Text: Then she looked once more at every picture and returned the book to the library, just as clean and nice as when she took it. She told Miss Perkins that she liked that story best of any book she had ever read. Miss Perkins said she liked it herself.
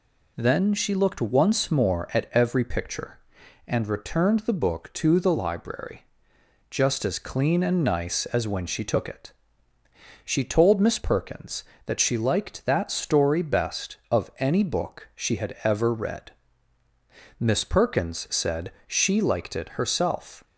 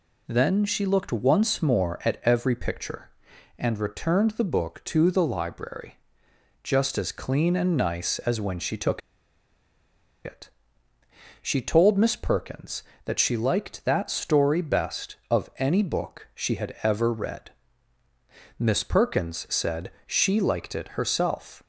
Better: first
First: pauses between "said" and "she"; slight; at 18.7 s; 0.16 s long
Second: pauses between "took" and "it"; strong; at 9.0 s; 1.2 s long // pauses between "said" and "she"; slight; at 19.8 s; 0.16 s long

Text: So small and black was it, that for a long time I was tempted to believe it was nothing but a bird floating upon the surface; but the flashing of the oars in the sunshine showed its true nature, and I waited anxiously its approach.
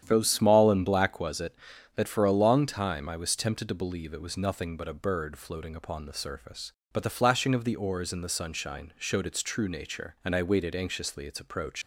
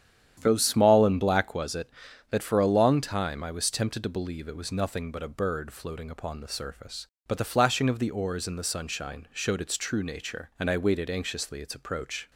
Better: second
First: starts louder than the rest; strong; until 1.0 s; 9.5 dB // leaves "approach" unfinished; at 11.8 s; 135 ms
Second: starts louder than the rest; strong; until 1.4 s; 9.5 dB

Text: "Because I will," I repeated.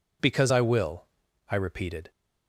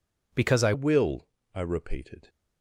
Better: first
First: none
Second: changes voice at "will"; from 0.7 s on; 1.5 s long

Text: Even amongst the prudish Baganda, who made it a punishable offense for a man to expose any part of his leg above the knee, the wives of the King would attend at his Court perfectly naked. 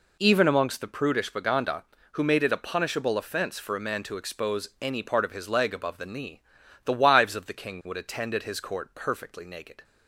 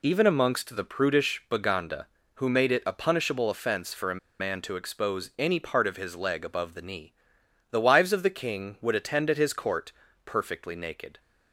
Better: first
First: none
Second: pauses between "a" and "man"; slight; at 4.1 s; 0.22 s long // pauses between "Court" and "perfectly"; slight; at 9.9 s; 0.34 s long

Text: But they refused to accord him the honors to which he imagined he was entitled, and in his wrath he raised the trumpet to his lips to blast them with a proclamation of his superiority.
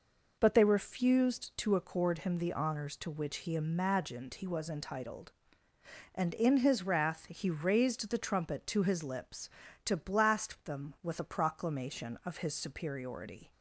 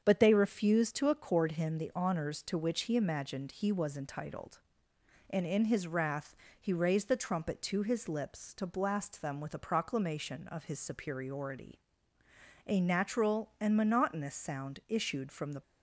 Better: first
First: none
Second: starts louder than the rest; strong; until 1.0 s; 7 dB // pauses between "wrath" and "he"; slight; at 6.3 s; 0.26 s long // goes on to say "A natural and monotonous sound issued from the"; strong; from 12.6 s on; 2.9 s long

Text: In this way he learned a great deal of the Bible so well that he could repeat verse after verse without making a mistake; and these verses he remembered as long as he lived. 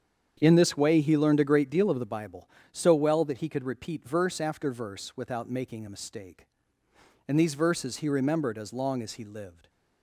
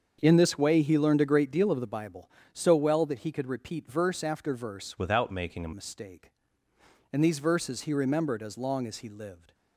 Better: first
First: starts louder than the rest; strong; until 1.4 s; 8 dB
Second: starts louder than the rest; until 1.2 s; 7 dB // changes voice from "without" to "a"; from 4.9 to 5.7 s; 0.8 s long

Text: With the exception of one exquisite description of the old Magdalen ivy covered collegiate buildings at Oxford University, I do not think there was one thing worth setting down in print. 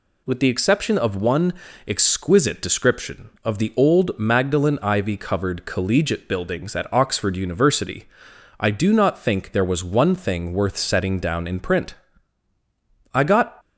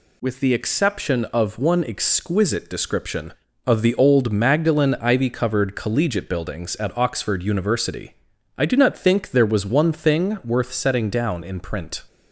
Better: second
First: pauses between "one" and "exquisite"; slight; at 1.5 s; 0.32 s long // goes on to say "I got"; slight; from 13.1 s on; 0.46 s long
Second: none

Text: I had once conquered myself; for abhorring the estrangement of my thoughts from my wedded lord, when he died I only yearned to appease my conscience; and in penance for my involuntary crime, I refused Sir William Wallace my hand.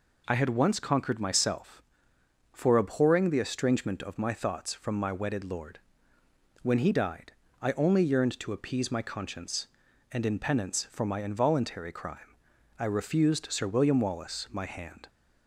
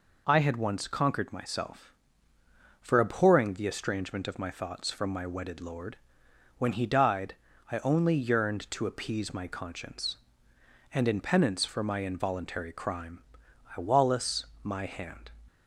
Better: first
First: pauses between "died" and "I"; slight; at 7.3 s; 0.28 s long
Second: pauses between "died" and "I"; slight; at 7.3 s; 0.36 s long // skips "refused Sir William"; at 13.8 s // pauses between "Wallace" and "my"; slight; at 14.4 s; 0.16 s long

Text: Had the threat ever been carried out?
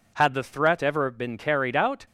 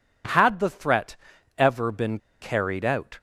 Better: first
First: none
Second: pauses between "threat" and "ever"; at 1.1 s; 0.40 s long // pauses between "been" and "carried"; slight; at 2.1 s; 0.23 s long

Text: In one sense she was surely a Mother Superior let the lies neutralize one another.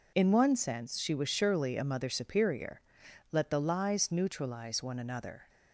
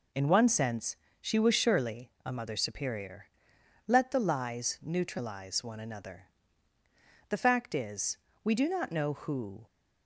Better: first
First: pauses between "Superior" and "let"; noticeable; at 2.8 s; 0.50 s long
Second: pauses between "sense" and "she"; slight; at 0.9 s; 0.24 s long // pauses between "Superior" and "let"; noticeable; at 3.2 s; 0.60 s long // goes on to say "The fact is we do not know who"; strong; from 7.2 s on; 2.3 s long

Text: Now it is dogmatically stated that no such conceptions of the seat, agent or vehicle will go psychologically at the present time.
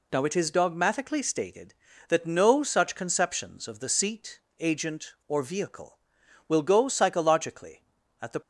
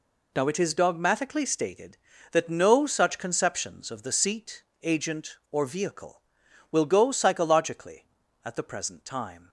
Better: second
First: stops before "present time"; at 8.4 s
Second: none

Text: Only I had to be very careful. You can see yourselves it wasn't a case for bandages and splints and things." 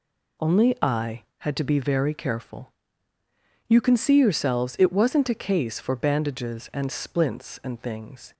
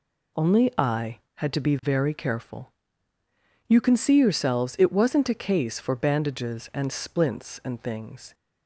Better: neither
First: none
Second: none

